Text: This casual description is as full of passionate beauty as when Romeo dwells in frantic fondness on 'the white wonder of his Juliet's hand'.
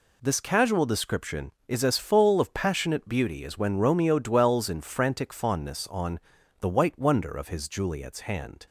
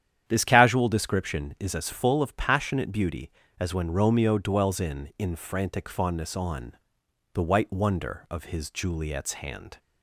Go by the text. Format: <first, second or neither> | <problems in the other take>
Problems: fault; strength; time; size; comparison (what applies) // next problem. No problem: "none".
first | starts louder than the rest; strong; until 1.2 s; 9.5 dB // says "in" twice; at 5.1 s // pauses between "on" and "the"; noticeable; at 6.7 s; 0.62 s long; also in the first